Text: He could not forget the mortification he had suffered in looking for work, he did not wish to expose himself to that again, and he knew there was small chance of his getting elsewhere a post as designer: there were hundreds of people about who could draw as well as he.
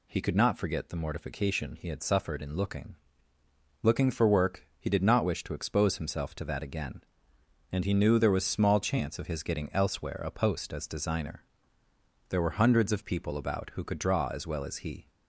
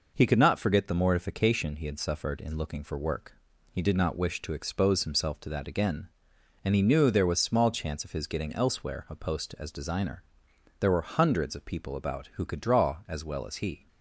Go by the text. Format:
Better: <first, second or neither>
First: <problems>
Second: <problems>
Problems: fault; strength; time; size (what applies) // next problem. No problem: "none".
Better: second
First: says "looking" twice; at 3.8 s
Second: none